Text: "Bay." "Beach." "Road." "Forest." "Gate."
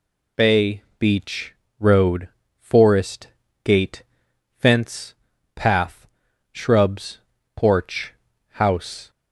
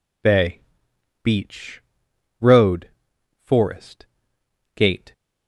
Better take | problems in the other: second | goes on to say "Fence Path Shrubs Porch House"; strong; from 4.5 s on; 4.5 s long

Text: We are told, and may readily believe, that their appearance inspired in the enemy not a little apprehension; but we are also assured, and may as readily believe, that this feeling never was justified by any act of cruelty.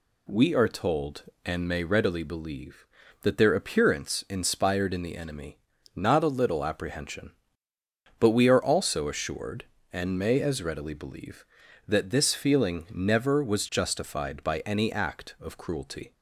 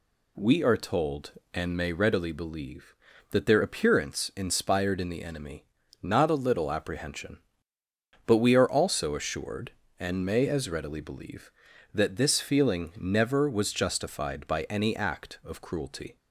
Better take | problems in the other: neither | pauses between "enemy" and "not"; the same in both

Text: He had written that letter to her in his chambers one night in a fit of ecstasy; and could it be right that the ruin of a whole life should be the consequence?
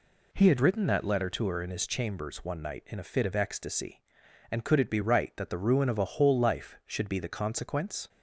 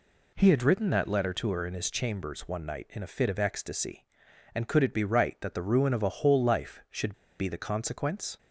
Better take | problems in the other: first | pauses between "should" and "be"; slight; at 7.1 s; 0.26 s long

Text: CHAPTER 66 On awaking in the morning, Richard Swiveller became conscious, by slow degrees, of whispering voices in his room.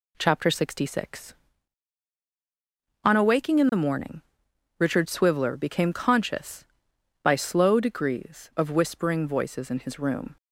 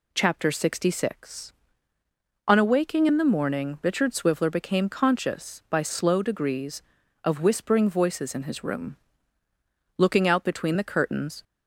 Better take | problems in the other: first | goes on to say "Looking out between the curtains"; from 9.9 s on; 1.4 s long

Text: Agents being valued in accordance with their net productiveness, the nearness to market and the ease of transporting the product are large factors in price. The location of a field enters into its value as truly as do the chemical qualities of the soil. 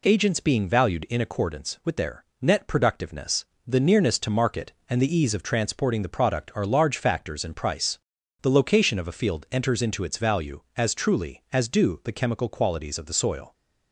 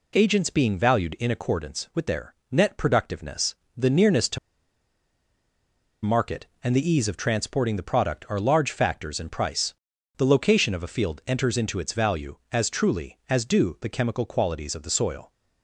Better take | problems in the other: first | pauses between "their" and "net"; slight; at 2.3 s; 0.16 s long; slight in the first // pauses between "to" and "market"; strong; at 4.3 s; 1.6 s long

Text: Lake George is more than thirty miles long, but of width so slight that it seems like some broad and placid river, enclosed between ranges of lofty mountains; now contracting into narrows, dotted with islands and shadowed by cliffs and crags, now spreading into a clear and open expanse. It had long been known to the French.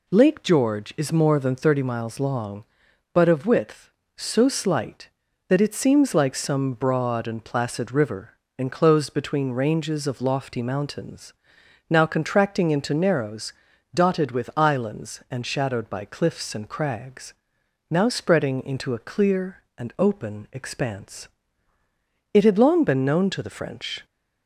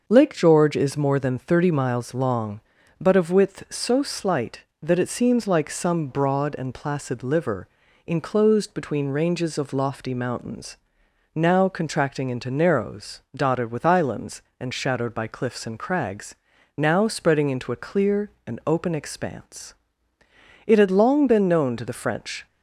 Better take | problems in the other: first | starts louder than the rest; until 1.0 s; 6.5 dB // says "liver" for "river"; at 7.2 s

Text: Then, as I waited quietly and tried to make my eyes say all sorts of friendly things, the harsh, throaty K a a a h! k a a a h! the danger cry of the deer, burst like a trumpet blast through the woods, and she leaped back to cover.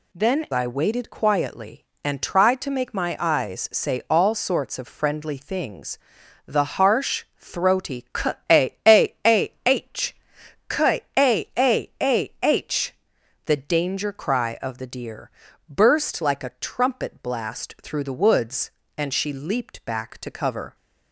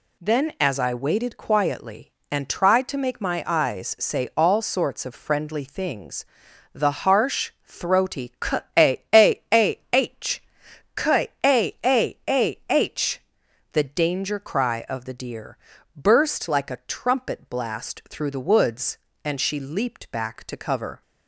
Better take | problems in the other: second | skips "as"; at 0.4 s // pauses between "K" and "a"; slight; at 8.3 s; 0.18 s long; slight in the second // pauses between "k" and "a"; slight; at 11.0 s; 0.16 s long; slight in the second

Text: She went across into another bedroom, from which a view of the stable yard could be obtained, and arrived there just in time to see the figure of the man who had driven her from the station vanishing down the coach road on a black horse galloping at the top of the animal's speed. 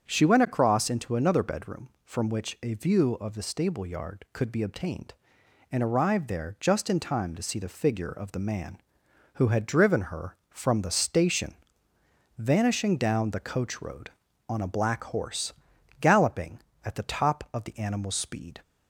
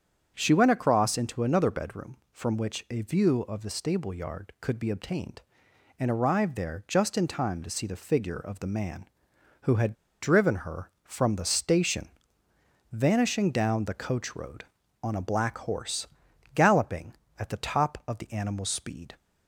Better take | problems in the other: first | starts louder than the rest; strong; until 1.3 s; 7.5 dB; strong in the first // pauses between "had" and "driven"; slight; at 9.9 s; 0.28 s long // pauses between "station" and "vanishing"; noticeable; at 12.0 s; 0.86 s long; noticeable in the first // pauses between "horse" and "galloping"; noticeable; at 16.0 s; 0.46 s long; noticeable in the first

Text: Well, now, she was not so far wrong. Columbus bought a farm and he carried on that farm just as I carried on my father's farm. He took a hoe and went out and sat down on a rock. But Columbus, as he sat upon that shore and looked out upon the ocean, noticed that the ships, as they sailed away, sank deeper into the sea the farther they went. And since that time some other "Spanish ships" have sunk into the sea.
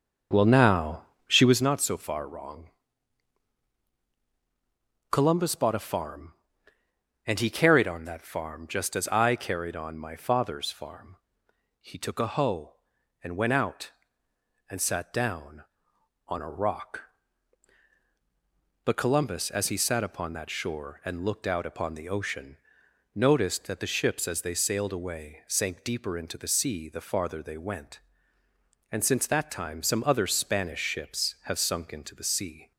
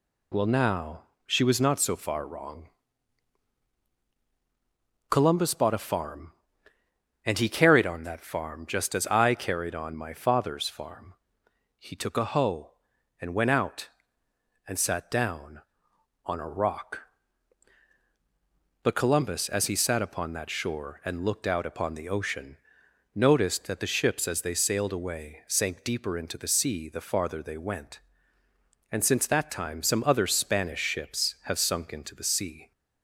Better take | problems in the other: second | starts louder than the rest; until 1.6 s; 6.5 dB

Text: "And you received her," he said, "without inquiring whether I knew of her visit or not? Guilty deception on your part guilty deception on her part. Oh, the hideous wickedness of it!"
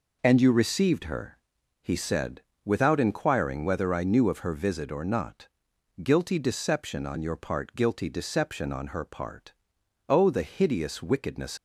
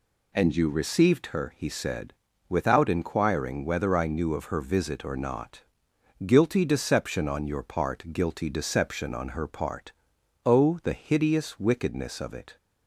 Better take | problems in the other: second | stops before "of it"; at 11.5 s

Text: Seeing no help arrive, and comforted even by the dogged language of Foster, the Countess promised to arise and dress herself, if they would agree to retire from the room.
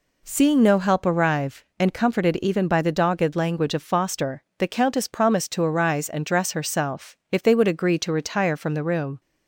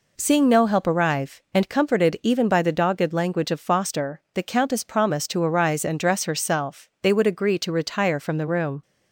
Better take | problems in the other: first | skips "if"; at 6.9 s

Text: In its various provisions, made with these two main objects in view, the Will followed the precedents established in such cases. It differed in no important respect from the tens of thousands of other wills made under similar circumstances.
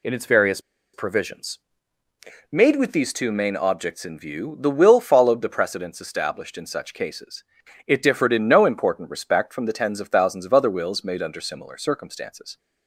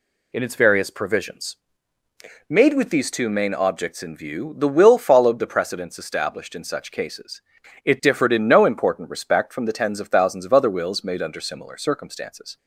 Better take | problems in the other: second | pauses between "various" and "provisions"; slight; at 0.5 s; 0.34 s long

